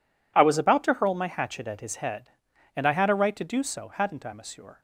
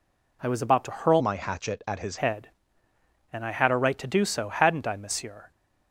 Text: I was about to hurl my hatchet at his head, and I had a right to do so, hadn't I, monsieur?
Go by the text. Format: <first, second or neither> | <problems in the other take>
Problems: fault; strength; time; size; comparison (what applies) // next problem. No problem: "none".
first | changes voice from "my" to "his"; from 1.2 to 2.1 s; 0.9 s long